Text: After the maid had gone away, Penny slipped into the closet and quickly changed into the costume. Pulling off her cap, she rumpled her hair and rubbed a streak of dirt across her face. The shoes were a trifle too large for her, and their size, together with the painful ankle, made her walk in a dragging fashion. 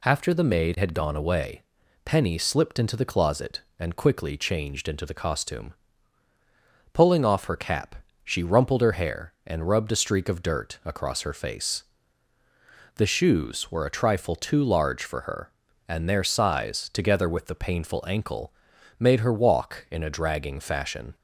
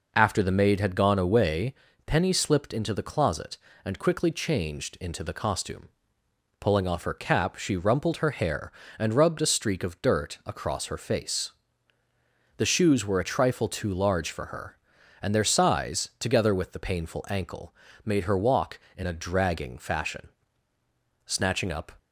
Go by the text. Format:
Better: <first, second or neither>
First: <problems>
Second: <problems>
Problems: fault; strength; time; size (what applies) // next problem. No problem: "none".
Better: first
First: none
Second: goes on to say "Snatching up"; noticeable; from 21.2 s on; 0.66 s long